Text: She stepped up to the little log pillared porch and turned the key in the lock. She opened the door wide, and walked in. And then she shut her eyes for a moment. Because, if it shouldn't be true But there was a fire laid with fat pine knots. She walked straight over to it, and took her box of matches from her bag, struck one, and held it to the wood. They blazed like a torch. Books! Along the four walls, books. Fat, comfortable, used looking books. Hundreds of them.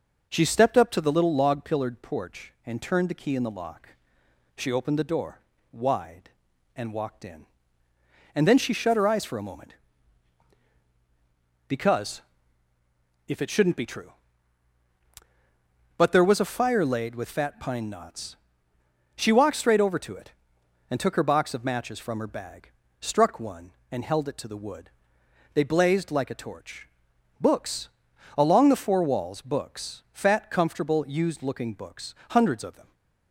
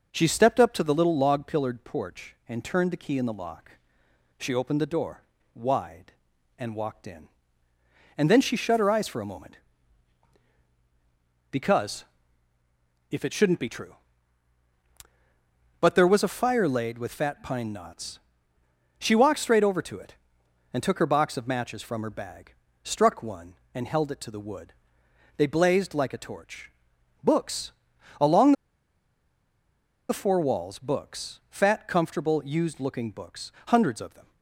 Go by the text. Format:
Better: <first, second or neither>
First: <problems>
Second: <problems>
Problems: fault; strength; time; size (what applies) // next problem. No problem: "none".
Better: first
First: pauses between "door" and "wide"; slight; at 5.3 s; 0.32 s long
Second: pauses between "door" and "wide"; slight; at 5.2 s; 0.32 s long // pauses between "Along" and "the"; strong; at 28.5 s; 1.5 s long